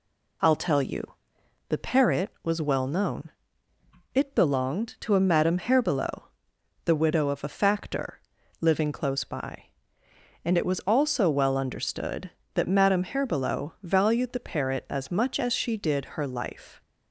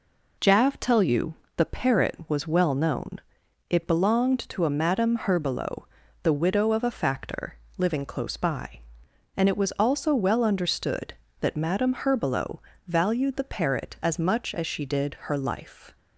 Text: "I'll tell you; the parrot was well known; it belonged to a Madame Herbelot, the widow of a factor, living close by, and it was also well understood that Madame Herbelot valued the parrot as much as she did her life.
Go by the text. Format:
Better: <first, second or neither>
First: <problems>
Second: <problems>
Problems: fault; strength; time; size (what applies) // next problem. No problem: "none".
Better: first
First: none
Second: says "Jav" for "I'll"; at 0.3 s // pauses between "Herbelot" and "valued"; slight; at 12.5 s; 0.26 s long